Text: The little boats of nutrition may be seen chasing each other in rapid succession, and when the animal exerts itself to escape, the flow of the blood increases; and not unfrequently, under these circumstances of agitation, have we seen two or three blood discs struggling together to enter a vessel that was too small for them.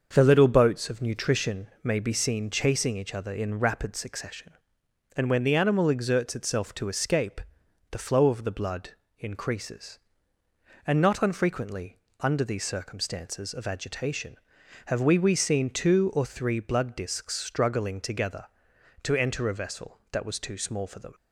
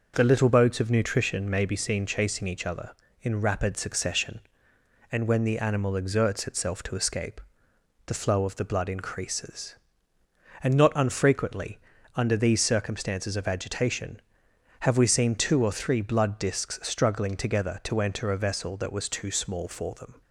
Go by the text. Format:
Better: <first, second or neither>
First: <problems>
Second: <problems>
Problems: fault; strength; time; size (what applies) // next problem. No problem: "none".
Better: second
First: starts louder than the rest; until 1.1 s; 6.5 dB // pauses between "blood" and "increases"; slight; at 8.8 s; 0.30 s long // says "we" twice; at 15.1 s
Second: none